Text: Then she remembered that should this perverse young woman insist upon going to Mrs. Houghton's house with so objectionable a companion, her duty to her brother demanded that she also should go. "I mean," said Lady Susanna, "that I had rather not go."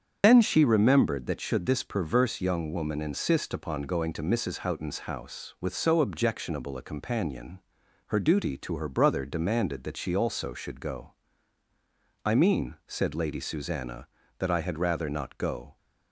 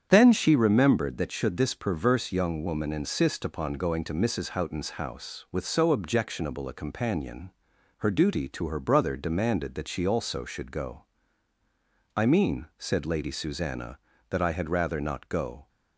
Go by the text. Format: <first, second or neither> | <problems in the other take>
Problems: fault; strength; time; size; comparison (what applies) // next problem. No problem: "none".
second | loses the start of "Then"; at 0.2 s; 50 ms // starts louder than the rest; strong; until 1.2 s; 7.5 dB; strong in the second